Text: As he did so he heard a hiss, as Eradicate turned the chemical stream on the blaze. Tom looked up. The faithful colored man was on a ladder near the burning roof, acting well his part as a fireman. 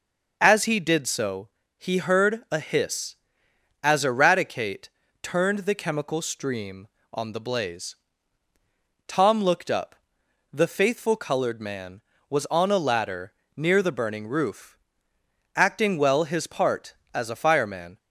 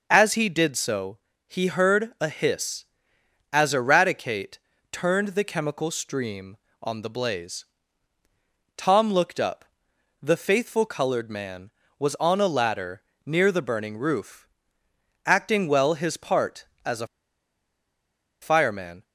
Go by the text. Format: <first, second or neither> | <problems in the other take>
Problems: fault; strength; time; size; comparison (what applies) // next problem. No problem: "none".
first | pauses between "so" and "he"; slight; at 1.1 s; 0.28 s long; slight in the first // pauses between "Eradicate" and "turned"; slight; at 4.5 s; 0.32 s long; slight in the first // pauses between "ladder" and "near"; slight; at 13.0 s; 0.24 s long; slight in the first // pauses between "a" and "fireman"; strong; at 17.0 s; 1.3 s long